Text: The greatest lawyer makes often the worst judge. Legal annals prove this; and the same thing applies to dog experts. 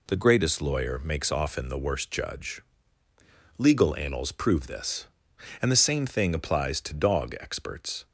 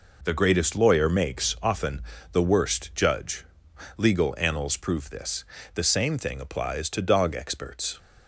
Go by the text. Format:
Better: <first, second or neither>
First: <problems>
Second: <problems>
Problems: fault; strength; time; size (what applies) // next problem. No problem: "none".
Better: first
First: none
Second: pauses between "often" and "the"; slight; at 1.9 s; 0.32 s long // skips "and"; at 5.5 s